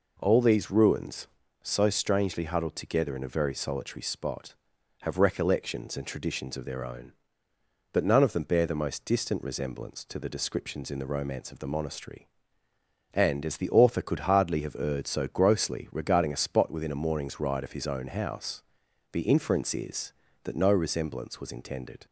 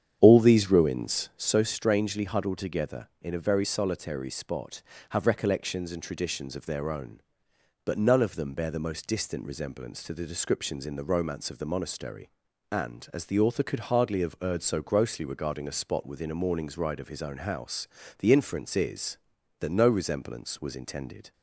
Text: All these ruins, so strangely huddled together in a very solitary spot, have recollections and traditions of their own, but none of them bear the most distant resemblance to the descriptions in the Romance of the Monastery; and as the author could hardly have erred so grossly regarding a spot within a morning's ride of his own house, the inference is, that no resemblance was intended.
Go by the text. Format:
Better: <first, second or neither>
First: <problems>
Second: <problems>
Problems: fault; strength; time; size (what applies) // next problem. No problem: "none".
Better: first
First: none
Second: starts louder than the rest; strong; until 1.5 s; 8.5 dB